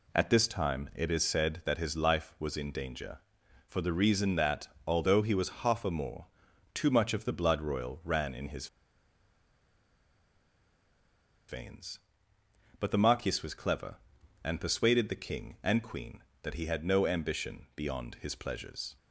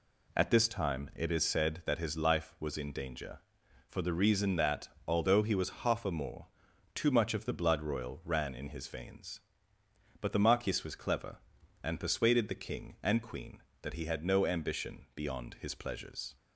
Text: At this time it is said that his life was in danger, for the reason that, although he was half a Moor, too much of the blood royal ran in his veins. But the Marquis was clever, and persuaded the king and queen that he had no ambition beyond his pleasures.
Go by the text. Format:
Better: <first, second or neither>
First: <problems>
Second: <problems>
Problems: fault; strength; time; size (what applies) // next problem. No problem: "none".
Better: second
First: pauses between "his" and "veins"; strong; at 8.6 s; 2.8 s long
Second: none